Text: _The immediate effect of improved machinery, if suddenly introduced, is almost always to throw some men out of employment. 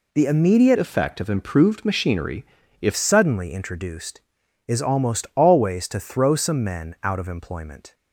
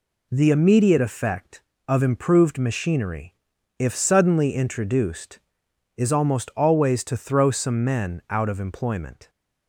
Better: second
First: changes voice from "effect" to "if"; from 0.7 to 2.9 s; 2.2 s long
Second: none

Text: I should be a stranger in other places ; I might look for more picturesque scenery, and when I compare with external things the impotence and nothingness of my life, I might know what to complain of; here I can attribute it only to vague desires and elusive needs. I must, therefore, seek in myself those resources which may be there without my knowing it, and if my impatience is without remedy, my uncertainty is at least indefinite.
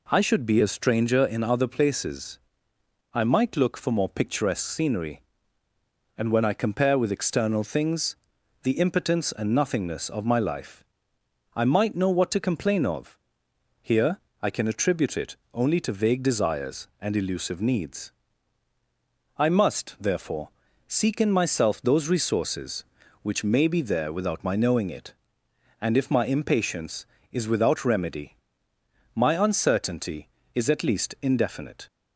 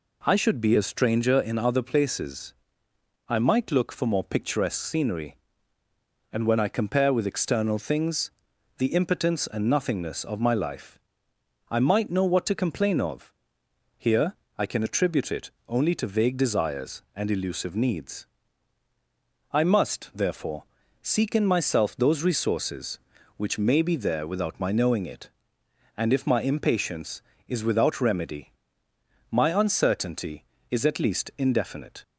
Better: neither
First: pauses between "things" and "the"; noticeable; at 8.1 s; 0.48 s long // pauses between "here" and "I"; slight; at 14.1 s; 0.22 s long // pauses between "it" and "only"; slight; at 15.3 s; 0.16 s long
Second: pauses between "things" and "the"; noticeable; at 8.2 s; 0.48 s long // pauses between "here" and "I"; slight; at 14.3 s; 0.22 s long // pauses between "it" and "only"; slight; at 15.5 s; 0.16 s long

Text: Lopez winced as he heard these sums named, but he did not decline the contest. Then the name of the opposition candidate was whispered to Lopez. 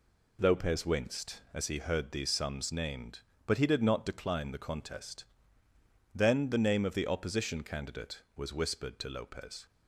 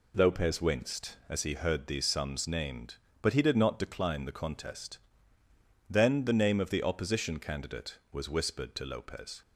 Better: neither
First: none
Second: none

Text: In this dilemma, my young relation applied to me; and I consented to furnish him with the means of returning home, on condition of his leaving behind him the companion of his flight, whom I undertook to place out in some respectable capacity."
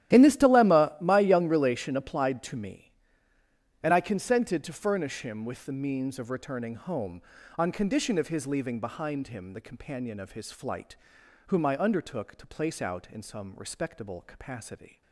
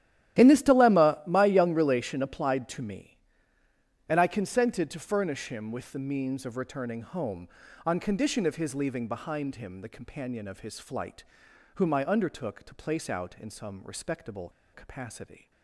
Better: first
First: starts louder than the rest; strong; until 1.2 s; 12.5 dB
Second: starts louder than the rest; strong; until 1.4 s; 12.5 dB // pauses between "respectable" and "capacity"; slight; at 14.4 s; 0.23 s long

